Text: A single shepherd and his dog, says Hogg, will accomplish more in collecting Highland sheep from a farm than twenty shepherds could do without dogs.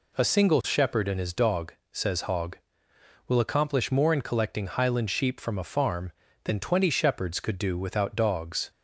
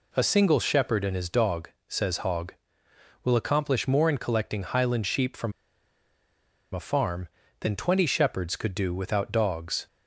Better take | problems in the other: first | pauses between "from" and "a"; at 5.5 s; 1.2 s long

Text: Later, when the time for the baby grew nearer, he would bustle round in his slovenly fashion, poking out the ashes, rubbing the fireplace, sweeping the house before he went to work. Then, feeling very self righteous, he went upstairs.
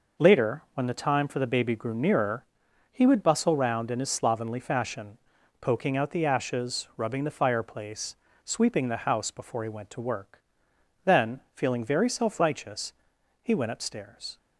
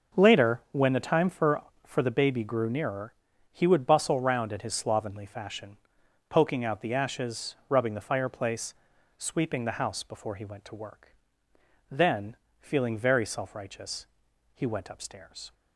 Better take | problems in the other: first | says "for" twice; at 1.8 s

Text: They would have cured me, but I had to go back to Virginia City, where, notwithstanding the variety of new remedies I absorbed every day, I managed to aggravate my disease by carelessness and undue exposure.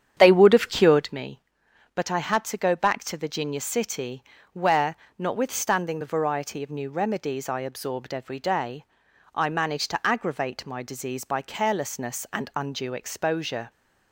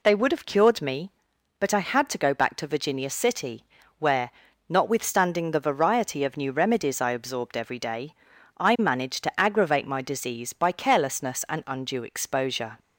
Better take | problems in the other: second | starts louder than the rest; strong; until 1.1 s; 9 dB

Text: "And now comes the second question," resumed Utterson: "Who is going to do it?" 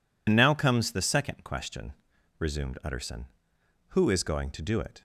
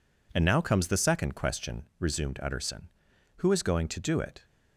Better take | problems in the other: second | loses the start of "And"; at 0.2 s; 75 ms

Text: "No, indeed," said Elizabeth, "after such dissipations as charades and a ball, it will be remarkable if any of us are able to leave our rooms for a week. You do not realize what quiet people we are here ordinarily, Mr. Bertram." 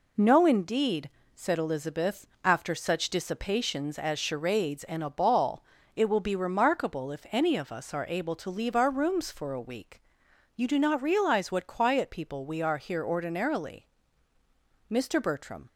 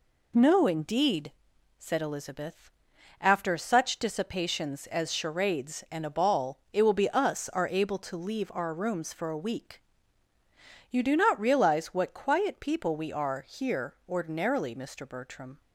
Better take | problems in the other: first | skips "remarkable if any of"; at 7.0 s

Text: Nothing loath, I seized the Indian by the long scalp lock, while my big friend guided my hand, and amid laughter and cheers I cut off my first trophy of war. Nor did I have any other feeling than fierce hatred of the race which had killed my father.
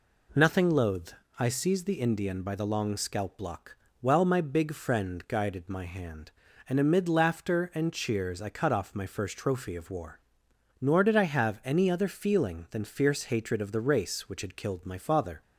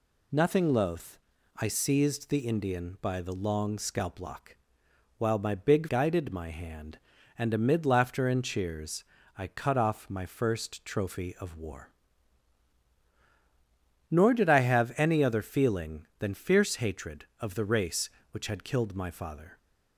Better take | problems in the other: first | skips "friend"; at 5.8 s // pauses between "cheers" and "I"; slight; at 9.0 s; 0.32 s long

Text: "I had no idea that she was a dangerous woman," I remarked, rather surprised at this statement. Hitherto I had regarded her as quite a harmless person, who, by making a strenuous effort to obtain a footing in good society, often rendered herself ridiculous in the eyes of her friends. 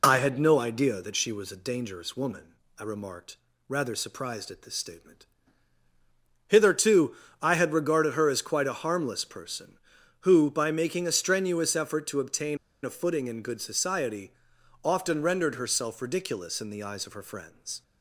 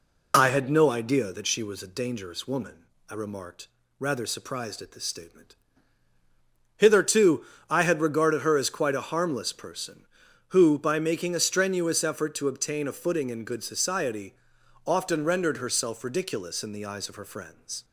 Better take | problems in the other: second | pauses between "Hitherto" and "I"; slight; at 7.1 s; 0.26 s long; slight in the second // pauses between "obtain" and "a"; slight; at 12.5 s; 0.26 s long

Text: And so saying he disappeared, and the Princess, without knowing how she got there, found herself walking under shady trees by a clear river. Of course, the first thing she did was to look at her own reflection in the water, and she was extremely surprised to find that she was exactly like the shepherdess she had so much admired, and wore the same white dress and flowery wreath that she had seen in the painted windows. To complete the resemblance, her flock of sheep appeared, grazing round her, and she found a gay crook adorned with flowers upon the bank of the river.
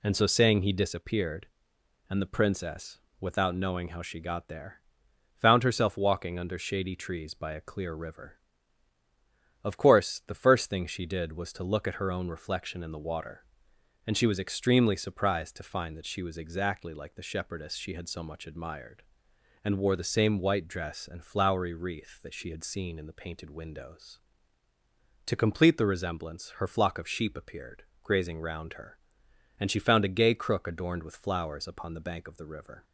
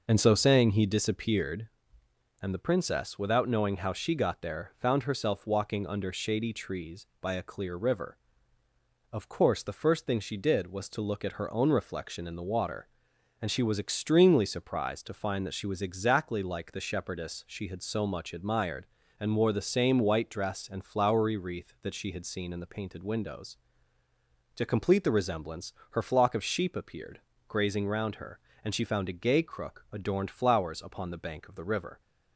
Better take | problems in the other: first | skips "with"; at 30.2 s

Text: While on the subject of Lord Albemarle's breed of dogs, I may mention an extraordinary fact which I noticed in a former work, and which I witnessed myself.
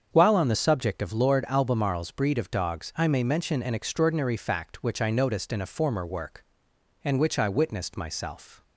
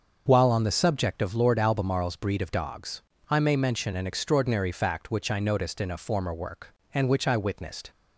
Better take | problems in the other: first | starts louder than the rest; until 1.2 s; 6.5 dB; strong in the first // stops before "myself"; at 7.9 s

